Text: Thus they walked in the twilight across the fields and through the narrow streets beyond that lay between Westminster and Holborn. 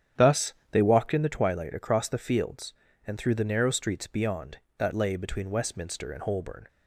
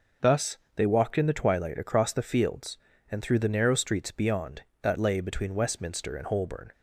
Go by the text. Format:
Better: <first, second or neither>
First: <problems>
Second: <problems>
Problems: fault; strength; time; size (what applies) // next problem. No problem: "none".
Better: second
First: starts louder than the rest; strong; until 1.2 s; 9.5 dB // pauses between "Thus" and "they"; slight; at 0.5 s; 0.18 s long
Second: pauses between "Thus" and "they"; slight; at 0.5 s; 0.18 s long